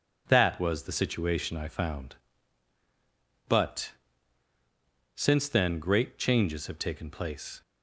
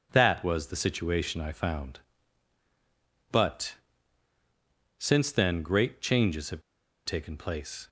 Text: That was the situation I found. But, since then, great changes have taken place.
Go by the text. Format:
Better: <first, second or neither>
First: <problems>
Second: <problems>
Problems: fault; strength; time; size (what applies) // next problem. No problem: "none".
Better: first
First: none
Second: pauses between "have" and "taken"; at 6.6 s; 0.44 s long